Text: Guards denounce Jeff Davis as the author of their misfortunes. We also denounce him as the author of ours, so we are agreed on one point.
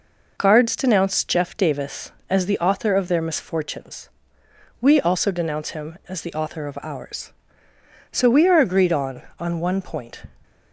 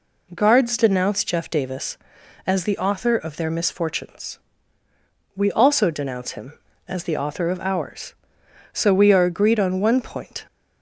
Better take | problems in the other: second | says "on" twice; at 9.3 s

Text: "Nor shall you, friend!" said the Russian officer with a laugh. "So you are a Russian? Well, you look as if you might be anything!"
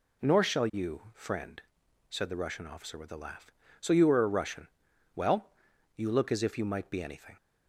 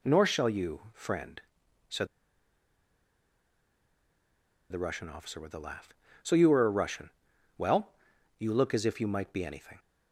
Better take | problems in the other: first | pauses between "said" and "the"; strong; at 2.0 s; 2.6 s long

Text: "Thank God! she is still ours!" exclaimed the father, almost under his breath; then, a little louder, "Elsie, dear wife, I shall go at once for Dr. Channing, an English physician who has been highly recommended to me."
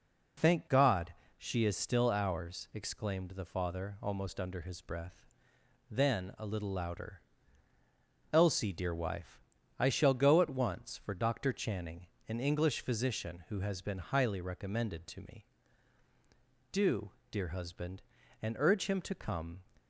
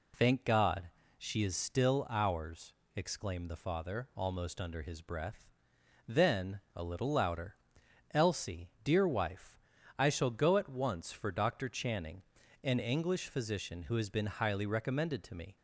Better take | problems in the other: second | goes on to say "Do dear husband and urge him to come"; strong; from 16.7 s on; 2.9 s long

